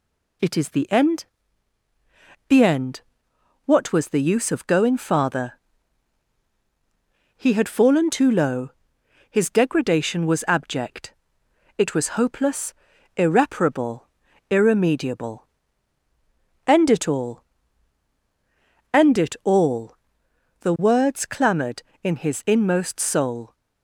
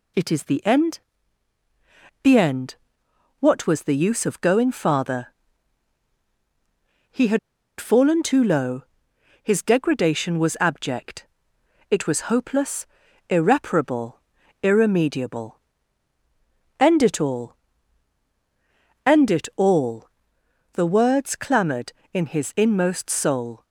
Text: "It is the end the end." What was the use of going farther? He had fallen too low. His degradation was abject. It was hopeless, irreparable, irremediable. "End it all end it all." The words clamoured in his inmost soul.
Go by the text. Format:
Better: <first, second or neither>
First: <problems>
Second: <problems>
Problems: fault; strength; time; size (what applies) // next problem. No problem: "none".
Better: first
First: pauses between "end" and "the"; at 1.2 s; 1.2 s long // pauses between "all" and "end"; strong; at 17.4 s; 1.4 s long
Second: pauses between "end" and "the"; at 0.9 s; 1.2 s long // pauses between "had" and "fallen"; at 7.3 s; 0.40 s long // pauses between "all" and "end"; strong; at 17.5 s; 1.4 s long